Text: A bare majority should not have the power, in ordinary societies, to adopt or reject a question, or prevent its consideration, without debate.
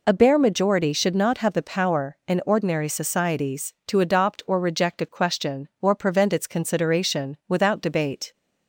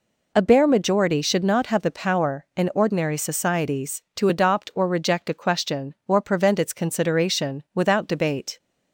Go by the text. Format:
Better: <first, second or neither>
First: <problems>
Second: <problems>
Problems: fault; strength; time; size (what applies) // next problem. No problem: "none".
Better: neither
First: none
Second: none